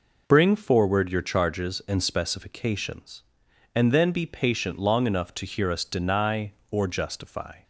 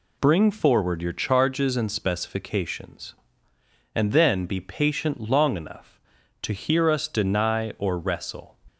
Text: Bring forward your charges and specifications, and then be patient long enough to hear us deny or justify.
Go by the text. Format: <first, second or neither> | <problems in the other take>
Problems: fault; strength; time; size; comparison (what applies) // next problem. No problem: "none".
first | says "wrestle" for "justify"; at 7.9 s